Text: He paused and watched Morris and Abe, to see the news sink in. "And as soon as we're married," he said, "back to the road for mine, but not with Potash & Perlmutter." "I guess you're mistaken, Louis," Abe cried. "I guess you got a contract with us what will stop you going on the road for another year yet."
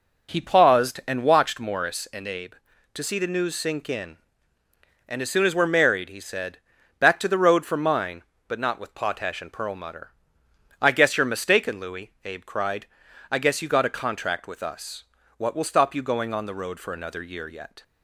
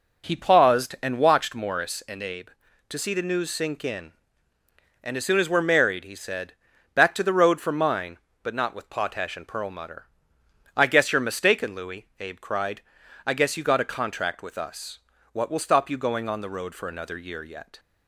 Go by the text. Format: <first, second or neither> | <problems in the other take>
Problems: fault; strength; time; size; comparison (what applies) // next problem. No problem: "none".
neither | pauses between "us" and "what"; slight; the same in both